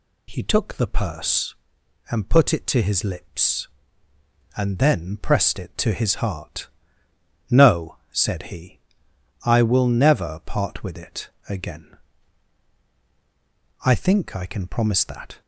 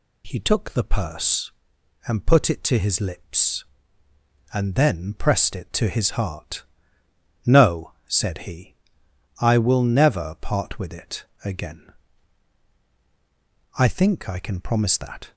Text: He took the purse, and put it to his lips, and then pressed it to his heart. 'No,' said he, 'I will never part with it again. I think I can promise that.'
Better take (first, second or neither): neither